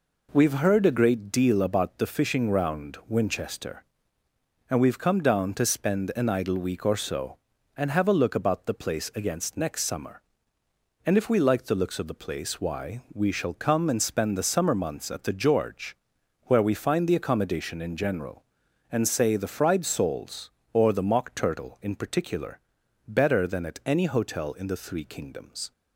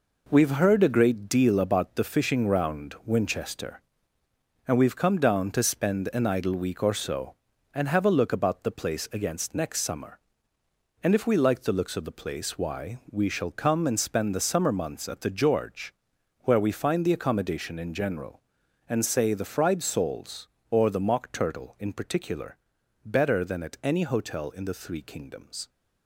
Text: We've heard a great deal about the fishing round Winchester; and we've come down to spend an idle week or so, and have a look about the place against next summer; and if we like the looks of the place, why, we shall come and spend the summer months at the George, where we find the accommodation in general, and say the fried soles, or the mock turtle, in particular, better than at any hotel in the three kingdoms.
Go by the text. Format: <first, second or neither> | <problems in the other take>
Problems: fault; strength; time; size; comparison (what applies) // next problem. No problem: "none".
first | gets quieter; strong; throughout; 8 dB